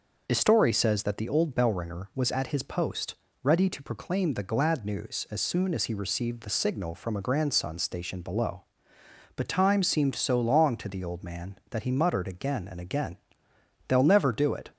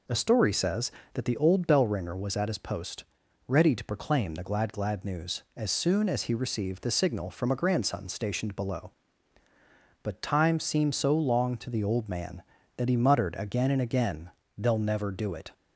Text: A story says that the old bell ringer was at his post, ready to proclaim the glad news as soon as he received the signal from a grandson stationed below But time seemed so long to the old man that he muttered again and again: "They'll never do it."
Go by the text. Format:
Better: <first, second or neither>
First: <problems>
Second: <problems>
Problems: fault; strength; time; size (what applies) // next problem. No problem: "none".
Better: first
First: none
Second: says "glad" twice; at 4.7 s